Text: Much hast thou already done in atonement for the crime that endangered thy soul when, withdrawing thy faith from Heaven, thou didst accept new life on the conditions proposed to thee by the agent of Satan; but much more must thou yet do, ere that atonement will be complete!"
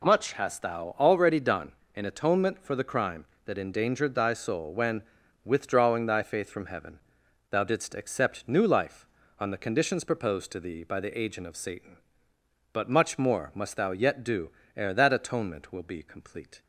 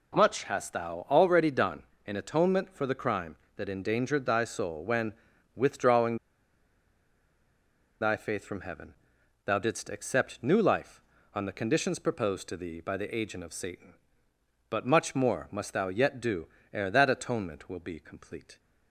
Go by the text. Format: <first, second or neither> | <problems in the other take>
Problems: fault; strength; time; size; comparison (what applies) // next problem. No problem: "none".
first | pauses between "withdrawing" and "thy"; strong; at 6.1 s; 1.8 s long